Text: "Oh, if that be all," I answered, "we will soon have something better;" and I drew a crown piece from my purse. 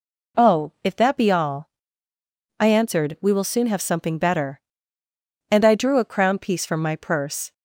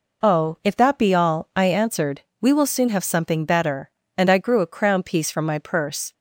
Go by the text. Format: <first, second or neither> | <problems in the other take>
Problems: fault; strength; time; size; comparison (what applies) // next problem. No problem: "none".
first | says "grew" for "drew"; at 4.3 s